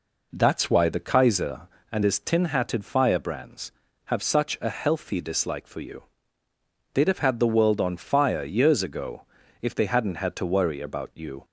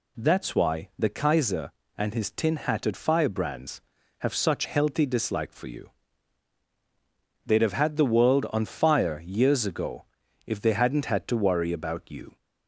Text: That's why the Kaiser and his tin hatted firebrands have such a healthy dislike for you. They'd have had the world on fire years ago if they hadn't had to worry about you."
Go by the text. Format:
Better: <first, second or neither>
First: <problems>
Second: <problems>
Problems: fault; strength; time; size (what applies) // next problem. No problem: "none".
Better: first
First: pauses between "ago" and "if"; slight; at 9.2 s; 0.36 s long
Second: skips "a"; at 4.6 s // pauses between "ago" and "if"; at 10.0 s; 0.40 s long